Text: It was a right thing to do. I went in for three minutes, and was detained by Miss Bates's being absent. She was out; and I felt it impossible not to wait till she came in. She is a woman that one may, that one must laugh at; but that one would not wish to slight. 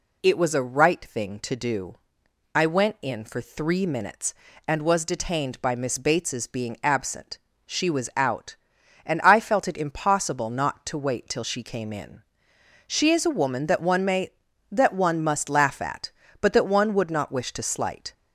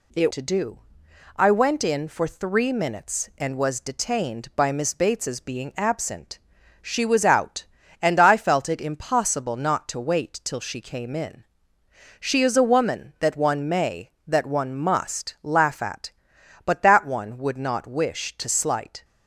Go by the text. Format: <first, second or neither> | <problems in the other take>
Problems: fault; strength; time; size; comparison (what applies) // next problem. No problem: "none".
first | skips "was a right thing"; at 0.3 s